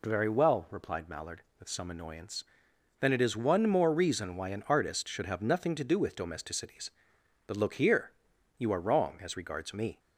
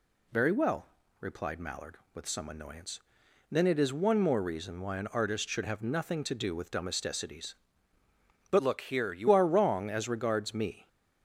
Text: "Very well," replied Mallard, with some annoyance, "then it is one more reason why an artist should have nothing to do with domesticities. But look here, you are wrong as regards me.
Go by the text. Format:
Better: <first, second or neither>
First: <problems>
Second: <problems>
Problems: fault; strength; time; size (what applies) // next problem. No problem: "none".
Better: first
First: none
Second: changes voice from "look" to "you"; from 8.5 to 9.2 s; 0.7 s long